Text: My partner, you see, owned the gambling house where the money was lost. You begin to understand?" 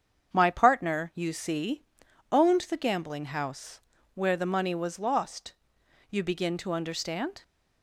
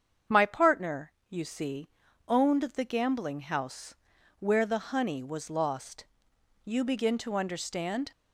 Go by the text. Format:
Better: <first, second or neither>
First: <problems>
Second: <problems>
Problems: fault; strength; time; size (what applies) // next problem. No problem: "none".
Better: first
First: starts louder than the rest; strong; until 1.3 s; 7.5 dB // pauses between "house" and "where"; slight; at 3.8 s; 0.32 s long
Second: starts louder than the rest; strong; until 1.4 s; 7.5 dB // pauses between "house" and "where"; at 3.9 s; 0.44 s long // says "honey" for "money"; at 4.9 s